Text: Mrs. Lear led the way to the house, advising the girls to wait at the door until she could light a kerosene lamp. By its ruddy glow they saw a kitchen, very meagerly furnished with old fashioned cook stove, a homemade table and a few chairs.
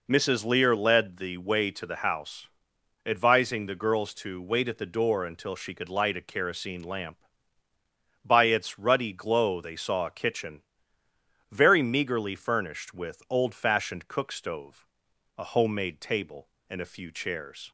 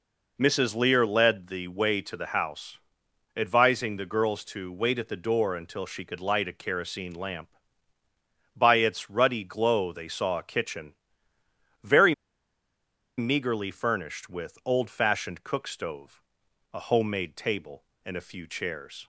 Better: first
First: none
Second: pauses between "very" and "meagerly"; at 12.1 s; 1.0 s long

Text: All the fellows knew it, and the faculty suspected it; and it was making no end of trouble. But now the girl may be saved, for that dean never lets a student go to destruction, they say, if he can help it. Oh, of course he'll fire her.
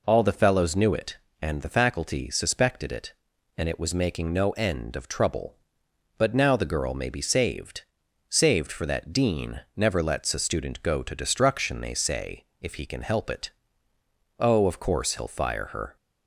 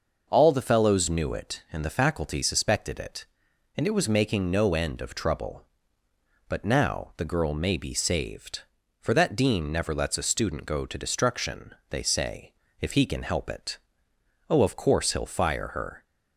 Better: second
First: says "saved" twice; at 8.2 s // pauses between "dean" and "never"; slight; at 9.5 s; 0.16 s long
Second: none

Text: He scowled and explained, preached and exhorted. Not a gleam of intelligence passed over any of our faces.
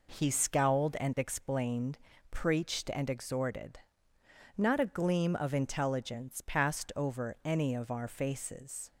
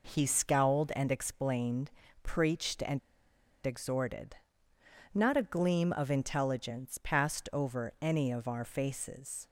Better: first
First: none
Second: pauses between "and" and "exhorted"; noticeable; at 2.9 s; 0.65 s long

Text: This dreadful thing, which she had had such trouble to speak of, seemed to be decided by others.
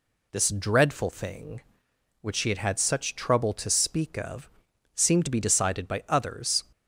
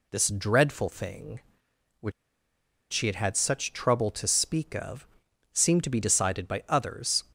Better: first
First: none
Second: pauses between "which" and "she"; noticeable; at 2.1 s; 0.80 s long

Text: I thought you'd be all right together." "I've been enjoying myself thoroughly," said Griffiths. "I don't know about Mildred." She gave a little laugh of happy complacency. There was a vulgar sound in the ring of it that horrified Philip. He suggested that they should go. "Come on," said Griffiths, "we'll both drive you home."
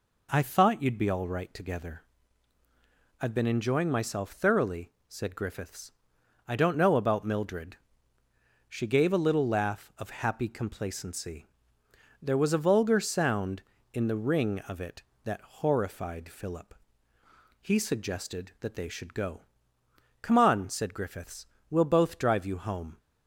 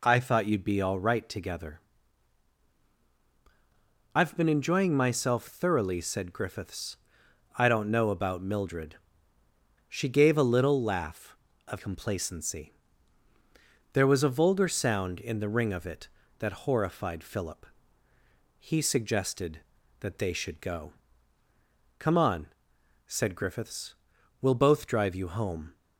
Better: first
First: none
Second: skips "happy"; at 11.7 s

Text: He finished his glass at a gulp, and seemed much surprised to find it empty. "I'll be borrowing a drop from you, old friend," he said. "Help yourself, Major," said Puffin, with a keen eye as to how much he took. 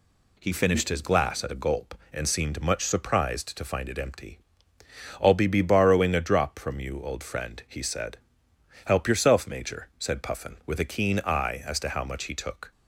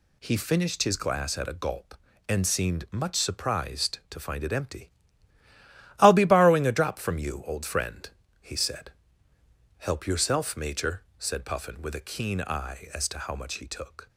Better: second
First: says "be" twice; at 5.4 s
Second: none

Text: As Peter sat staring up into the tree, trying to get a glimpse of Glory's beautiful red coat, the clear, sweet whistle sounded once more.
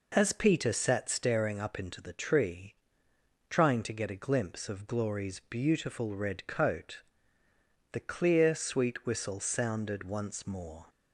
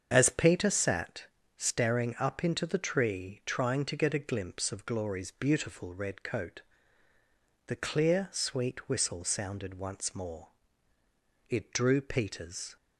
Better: first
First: none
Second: starts louder than the rest; strong; until 1.1 s; 7.5 dB // pauses between "sat" and "staring"; slight; at 1.2 s; 0.34 s long // goes on to say "It drew Peter's"; noticeable; from 11.4 s on; 1.2 s long

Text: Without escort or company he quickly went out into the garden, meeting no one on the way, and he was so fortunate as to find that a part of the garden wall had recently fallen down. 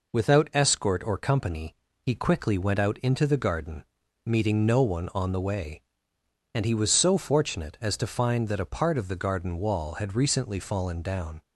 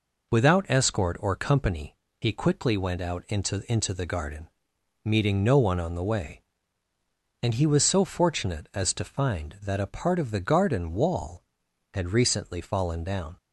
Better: first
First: pauses between "company" and "he"; slight; at 1.7 s; 0.26 s long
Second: pauses between "company" and "he"; slight; at 1.9 s; 0.24 s long // says "into" twice; at 3.7 s

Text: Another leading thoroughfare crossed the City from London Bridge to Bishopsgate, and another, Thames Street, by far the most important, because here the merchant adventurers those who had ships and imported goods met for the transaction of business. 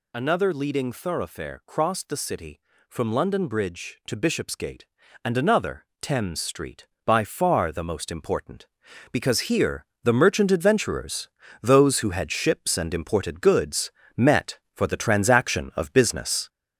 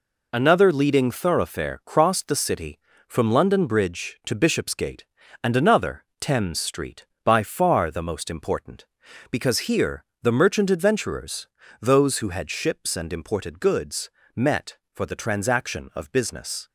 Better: second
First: gets louder; noticeable; throughout; 4.5 dB // pauses between "here" and "the"; slight; at 9.8 s; 0.20 s long // pauses between "adventurers" and "those"; slight; at 11.2 s; 0.32 s long // pauses between "goods" and "met"; slight; at 13.9 s; 0.26 s long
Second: pauses between "here" and "the"; slight; at 10.0 s; 0.20 s long // pauses between "adventurers" and "those"; slight; at 11.4 s; 0.32 s long // pauses between "goods" and "met"; slight; at 14.0 s; 0.26 s long

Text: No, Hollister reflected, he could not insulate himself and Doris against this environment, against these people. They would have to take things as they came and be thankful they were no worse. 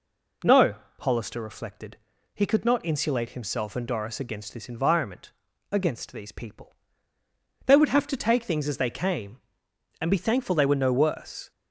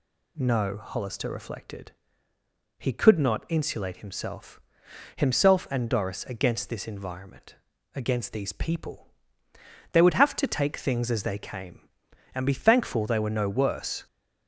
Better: first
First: none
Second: says "himself" twice; at 5.1 s

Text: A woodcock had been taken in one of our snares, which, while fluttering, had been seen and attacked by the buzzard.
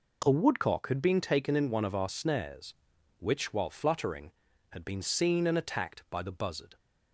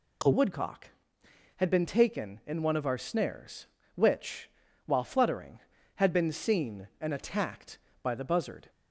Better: first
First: none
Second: changes voice at "woodcock"; from 0.3 s on; 8.3 s long

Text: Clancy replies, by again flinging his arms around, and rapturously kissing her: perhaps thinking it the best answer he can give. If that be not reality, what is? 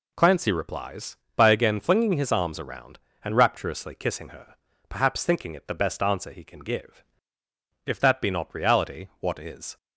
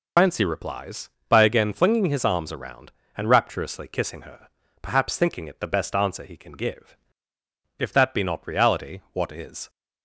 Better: first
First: none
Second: loses the start of "Clancy"; at 0.1 s; 95 ms

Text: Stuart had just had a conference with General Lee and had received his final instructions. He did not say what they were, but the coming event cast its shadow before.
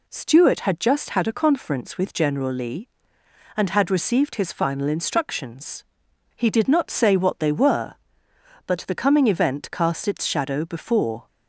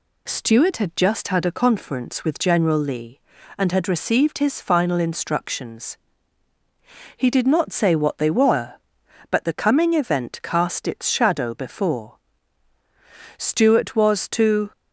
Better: first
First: none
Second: goes on to say "Stuart was to"; from 13.3 s on; 1.3 s long

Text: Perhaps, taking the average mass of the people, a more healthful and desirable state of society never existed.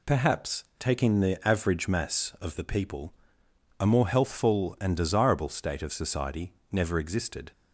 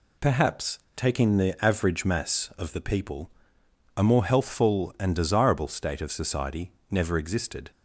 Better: neither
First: pauses between "society" and "never"; slight; at 6.5 s; 0.18 s long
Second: pauses between "society" and "never"; slight; at 6.7 s; 0.18 s long

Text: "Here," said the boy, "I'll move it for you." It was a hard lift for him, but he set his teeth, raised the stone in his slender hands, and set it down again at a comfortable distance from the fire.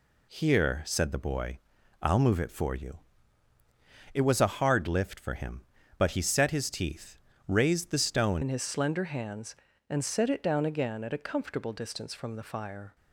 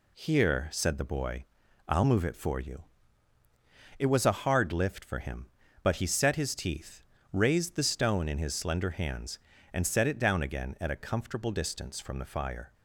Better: second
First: changes voice at "in"; from 8.4 s on; 4.5 s long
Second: none

